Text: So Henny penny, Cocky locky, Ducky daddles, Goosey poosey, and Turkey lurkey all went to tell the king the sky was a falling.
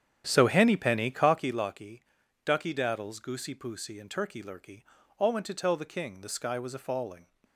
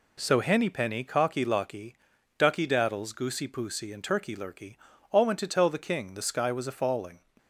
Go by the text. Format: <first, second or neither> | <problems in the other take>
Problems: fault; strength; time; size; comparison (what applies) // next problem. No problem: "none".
second | starts louder than the rest; strong; until 1.6 s; 9 dB // pauses between "lurkey" and "all"; at 4.8 s; 0.38 s long; also in the second